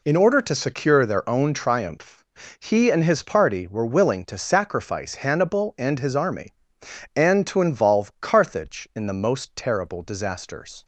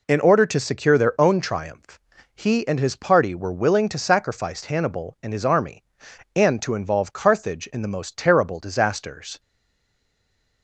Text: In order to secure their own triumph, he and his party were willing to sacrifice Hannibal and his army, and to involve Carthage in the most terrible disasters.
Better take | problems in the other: first | stays silent after the last word; noticeable; from 9.3 s on; 1.3 s long

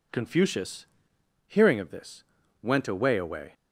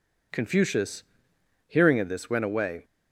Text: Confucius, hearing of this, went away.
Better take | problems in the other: second | says "away" twice; at 3.1 s

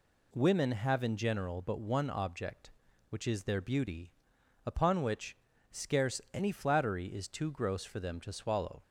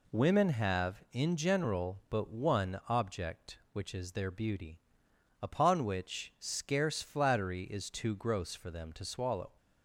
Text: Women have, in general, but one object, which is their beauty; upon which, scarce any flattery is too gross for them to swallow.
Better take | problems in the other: first | skips "any"; at 7.0 s

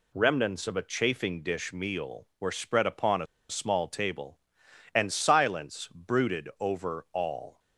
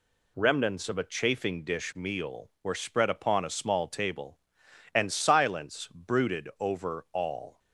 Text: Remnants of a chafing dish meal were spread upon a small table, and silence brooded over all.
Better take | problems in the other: second | pauses between "a" and "small"; slight; at 3.2 s; 0.23 s long

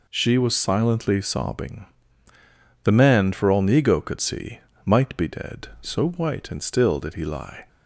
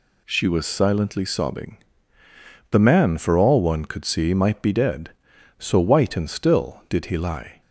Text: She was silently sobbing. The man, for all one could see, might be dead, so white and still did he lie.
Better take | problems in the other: second | says "nego" for "one"; at 3.6 s

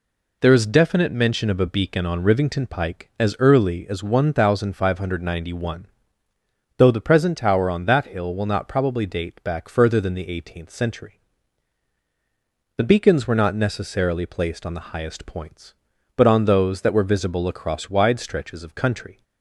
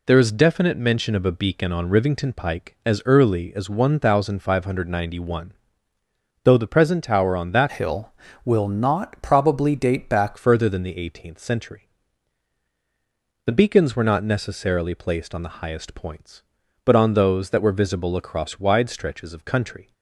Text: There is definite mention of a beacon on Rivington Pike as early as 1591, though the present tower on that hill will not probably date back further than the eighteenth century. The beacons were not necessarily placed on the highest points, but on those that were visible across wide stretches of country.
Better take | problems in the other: first | changes voice from "hill" to "back"; from 7.7 to 10.3 s; 2.6 s long

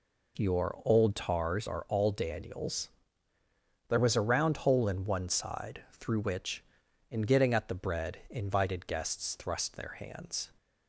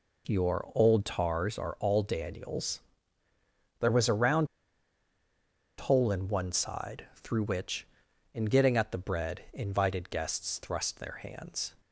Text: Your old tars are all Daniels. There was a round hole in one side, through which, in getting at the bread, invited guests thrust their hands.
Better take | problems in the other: first | pauses between "round" and "hole"; strong; at 4.4 s; 1.3 s long

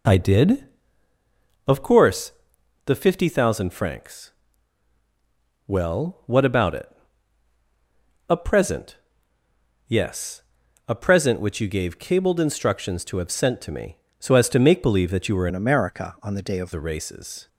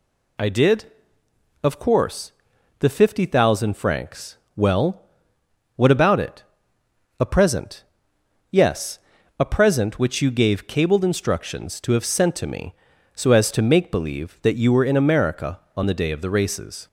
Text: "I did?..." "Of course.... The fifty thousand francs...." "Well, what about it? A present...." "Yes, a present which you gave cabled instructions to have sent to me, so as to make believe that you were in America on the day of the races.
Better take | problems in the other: second | changes voice from "in" to "of"; from 15.4 to 16.7 s; 1.3 s long

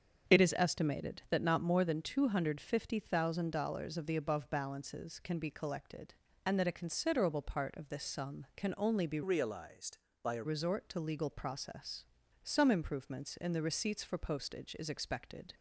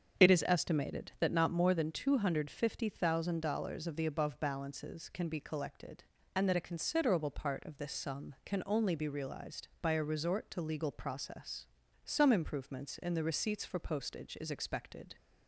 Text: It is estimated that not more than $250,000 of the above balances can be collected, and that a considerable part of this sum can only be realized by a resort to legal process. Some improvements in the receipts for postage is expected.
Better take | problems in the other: second | starts louder than the rest; strong; until 1.4 s; 7.5 dB; strong in the second // changes voice from "realized" to "a"; from 9.2 to 10.4 s; 1.2 s long

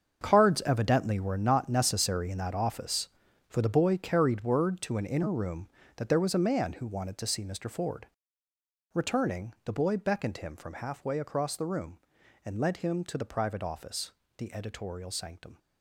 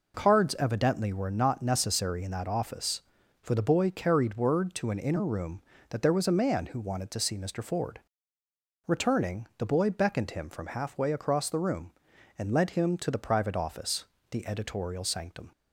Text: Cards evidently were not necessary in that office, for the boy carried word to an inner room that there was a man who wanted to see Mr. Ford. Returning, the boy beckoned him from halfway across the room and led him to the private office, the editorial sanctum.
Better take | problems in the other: second | gets quieter; strong; throughout; 12 dB

